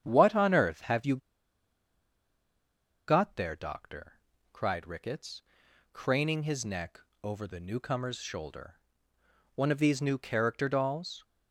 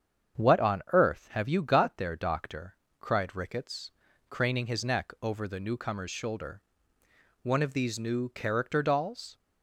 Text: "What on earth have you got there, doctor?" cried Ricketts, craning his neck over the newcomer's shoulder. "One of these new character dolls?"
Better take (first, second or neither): second